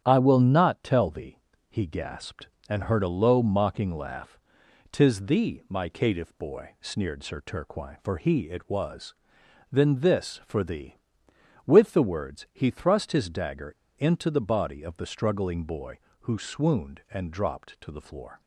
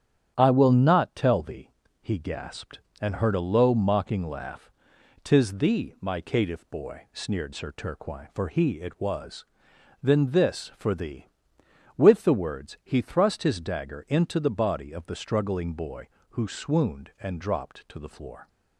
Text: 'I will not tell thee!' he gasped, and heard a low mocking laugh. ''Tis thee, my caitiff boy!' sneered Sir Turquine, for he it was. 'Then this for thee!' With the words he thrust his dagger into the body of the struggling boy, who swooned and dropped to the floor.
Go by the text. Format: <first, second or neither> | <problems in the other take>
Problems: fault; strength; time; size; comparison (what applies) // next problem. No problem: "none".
second | starts louder than the rest; strong; until 1.0 s; 9 dB; strong in the second // pauses between "dagger" and "into"; slight; at 13.7 s; 0.24 s long